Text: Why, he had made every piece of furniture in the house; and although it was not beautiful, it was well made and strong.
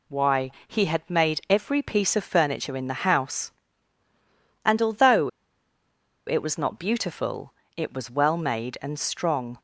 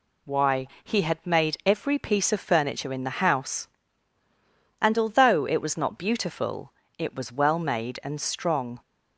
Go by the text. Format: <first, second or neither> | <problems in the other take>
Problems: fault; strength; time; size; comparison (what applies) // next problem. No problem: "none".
second | pauses between "although" and "it"; at 5.2 s; 0.98 s long